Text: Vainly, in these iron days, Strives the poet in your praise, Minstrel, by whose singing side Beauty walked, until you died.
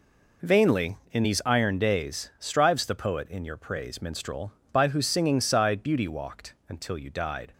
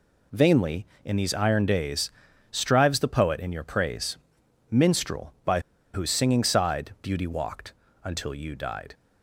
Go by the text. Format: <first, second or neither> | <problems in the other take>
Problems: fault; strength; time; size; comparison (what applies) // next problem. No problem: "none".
first | pauses between "by" and "whose"; slight; at 5.5 s; 0.33 s long